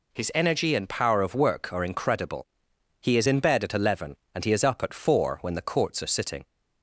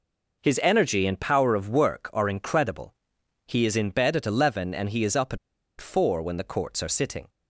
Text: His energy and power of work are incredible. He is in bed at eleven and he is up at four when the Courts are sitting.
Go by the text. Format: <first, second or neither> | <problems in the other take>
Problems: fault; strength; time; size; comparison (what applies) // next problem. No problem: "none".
first | pauses between "at" and "four"; at 5.3 s; 0.42 s long